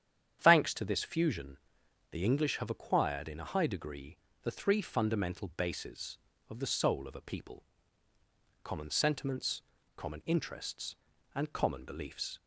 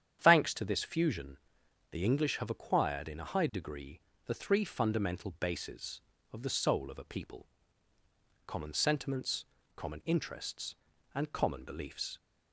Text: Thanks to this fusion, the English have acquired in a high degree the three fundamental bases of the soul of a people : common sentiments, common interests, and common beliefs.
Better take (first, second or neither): neither